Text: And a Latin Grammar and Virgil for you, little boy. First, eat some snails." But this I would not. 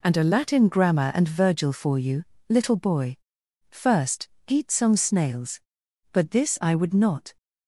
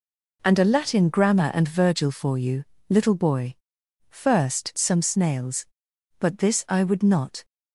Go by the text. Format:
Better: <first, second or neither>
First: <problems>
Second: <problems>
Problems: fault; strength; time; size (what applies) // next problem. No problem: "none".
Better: first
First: none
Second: skips "eat"; at 4.7 s